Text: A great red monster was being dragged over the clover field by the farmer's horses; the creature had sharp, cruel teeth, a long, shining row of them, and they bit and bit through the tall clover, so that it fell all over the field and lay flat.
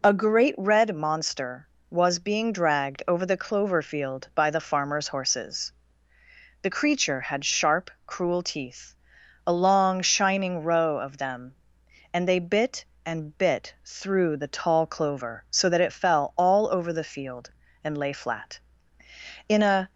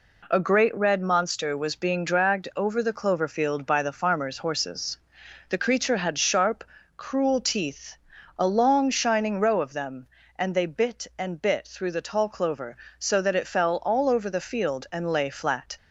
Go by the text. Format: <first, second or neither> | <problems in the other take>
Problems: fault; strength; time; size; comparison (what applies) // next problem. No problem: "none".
second | goes on to say "In a"; slight; from 19.5 s on; 0.40 s long